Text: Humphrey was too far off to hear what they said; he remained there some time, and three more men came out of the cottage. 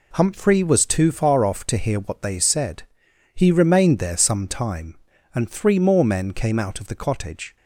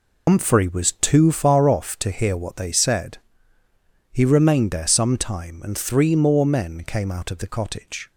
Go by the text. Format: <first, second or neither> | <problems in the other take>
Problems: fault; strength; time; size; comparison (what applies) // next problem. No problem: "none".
first | loses the start of "Humphrey"; at 0.2 s; 100 ms